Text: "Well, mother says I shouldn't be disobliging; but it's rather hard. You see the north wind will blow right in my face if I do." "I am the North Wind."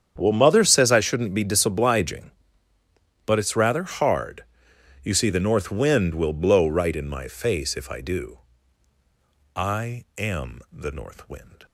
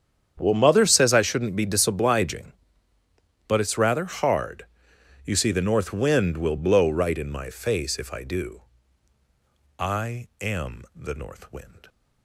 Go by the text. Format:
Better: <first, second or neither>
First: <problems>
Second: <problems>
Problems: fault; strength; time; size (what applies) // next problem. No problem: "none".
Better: neither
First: starts louder than the rest; strong; until 1.1 s; 8.5 dB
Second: starts louder than the rest; strong; until 1.3 s; 8.5 dB